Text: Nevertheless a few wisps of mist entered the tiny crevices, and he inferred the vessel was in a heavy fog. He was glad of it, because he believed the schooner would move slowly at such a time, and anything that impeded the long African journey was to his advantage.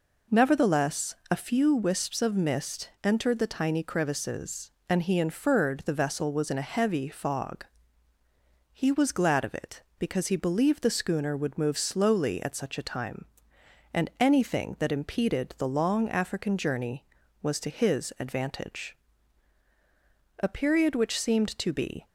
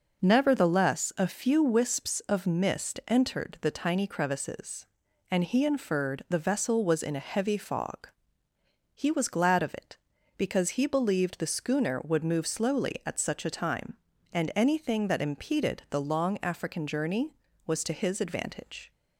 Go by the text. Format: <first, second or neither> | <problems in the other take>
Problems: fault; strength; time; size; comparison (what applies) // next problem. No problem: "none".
second | pauses between "Nevertheless" and "a"; slight; at 1.1 s; 0.16 s long // goes on to say "A period which seemed to be"; from 20.4 s on; 1.6 s long